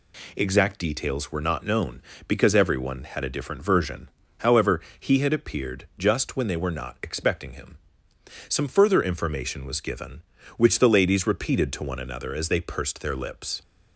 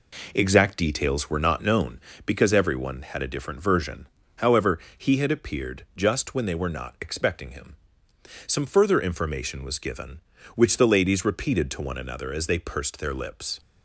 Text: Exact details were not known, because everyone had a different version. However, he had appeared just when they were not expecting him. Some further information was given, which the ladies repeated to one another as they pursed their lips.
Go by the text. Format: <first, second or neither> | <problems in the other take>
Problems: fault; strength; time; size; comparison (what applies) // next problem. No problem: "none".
first | starts louder than the rest; until 2.0 s; 3.5 dB